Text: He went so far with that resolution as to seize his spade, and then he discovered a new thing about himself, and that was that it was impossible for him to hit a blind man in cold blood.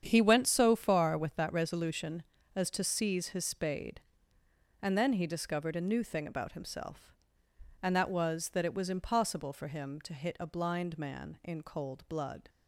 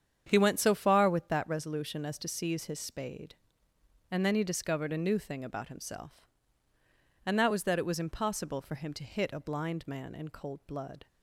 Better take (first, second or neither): neither